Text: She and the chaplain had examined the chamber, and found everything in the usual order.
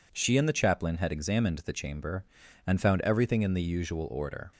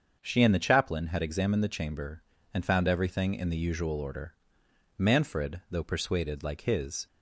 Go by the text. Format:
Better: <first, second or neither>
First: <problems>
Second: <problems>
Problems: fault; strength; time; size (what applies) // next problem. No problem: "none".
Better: first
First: none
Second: starts louder than the rest; until 1.2 s; 7 dB // goes on to say "Manfred though persuaded like his"; strong; from 4.9 s on; 2.1 s long